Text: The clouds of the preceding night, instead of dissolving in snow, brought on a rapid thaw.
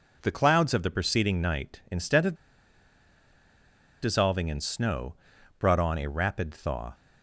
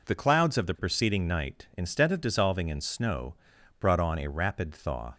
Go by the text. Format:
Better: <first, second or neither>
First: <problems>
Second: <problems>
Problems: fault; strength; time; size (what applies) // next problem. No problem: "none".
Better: second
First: pauses between "of" and "dissolving"; strong; at 2.3 s; 1.6 s long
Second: none